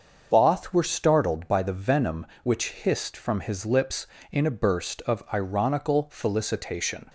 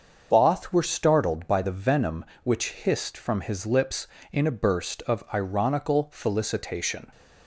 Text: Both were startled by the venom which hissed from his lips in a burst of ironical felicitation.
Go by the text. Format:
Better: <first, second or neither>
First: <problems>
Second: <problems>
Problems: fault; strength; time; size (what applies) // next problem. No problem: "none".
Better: neither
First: starts louder than the rest; until 1.3 s; 6.5 dB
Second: starts louder than the rest; until 1.3 s; 6.5 dB